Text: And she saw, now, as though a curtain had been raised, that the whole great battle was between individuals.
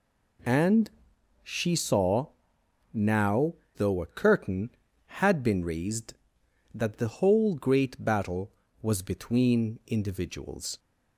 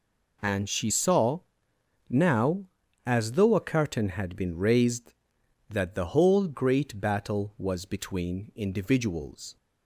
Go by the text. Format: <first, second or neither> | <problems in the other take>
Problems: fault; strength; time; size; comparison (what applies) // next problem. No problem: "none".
second | pauses between "And" and "she"; noticeable; at 0.8 s; 0.54 s long // skips "as"; at 3.6 s